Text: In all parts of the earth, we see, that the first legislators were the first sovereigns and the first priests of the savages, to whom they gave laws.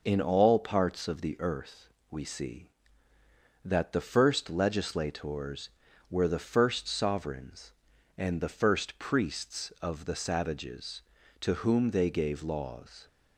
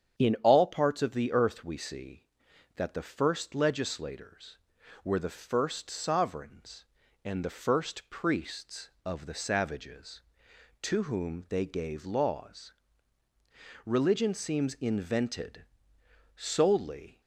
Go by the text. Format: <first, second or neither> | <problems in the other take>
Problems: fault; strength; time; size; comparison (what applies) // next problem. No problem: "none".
first | starts louder than the rest; strong; until 1.2 s; 8.5 dB // goes on to say "Religion seems invented solely"; strong; from 13.8 s on; 3.3 s long